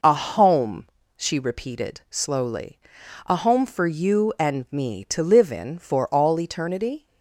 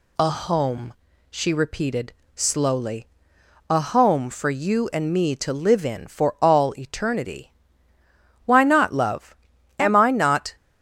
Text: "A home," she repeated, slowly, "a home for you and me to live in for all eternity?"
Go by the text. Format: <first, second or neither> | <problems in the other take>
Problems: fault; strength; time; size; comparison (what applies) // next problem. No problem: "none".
first | goes on to say "Why not love Am I not"; strong; from 8.4 s on; 2.1 s long